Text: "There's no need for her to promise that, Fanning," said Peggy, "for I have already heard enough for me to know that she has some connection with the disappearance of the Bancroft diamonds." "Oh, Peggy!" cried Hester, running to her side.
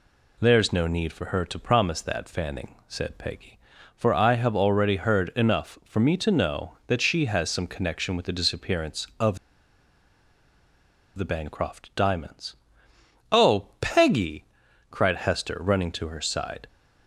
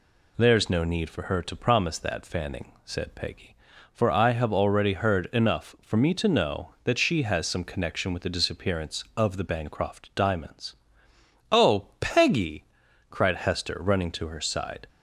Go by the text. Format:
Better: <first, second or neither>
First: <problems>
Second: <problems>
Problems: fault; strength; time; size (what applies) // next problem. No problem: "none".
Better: second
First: pauses between "of" and "the"; strong; at 9.3 s; 1.8 s long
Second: none